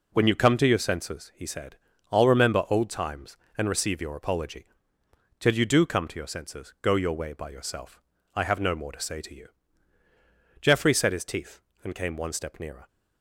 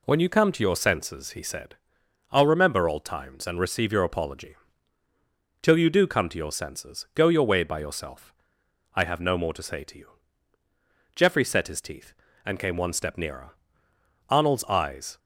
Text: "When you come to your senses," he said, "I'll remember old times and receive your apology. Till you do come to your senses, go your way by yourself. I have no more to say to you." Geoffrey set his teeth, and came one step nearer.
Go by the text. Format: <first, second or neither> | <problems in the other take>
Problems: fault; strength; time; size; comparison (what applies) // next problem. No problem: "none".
first | goes on to say "Arnold's eyes"; noticeable; from 14.2 s on; 0.90 s long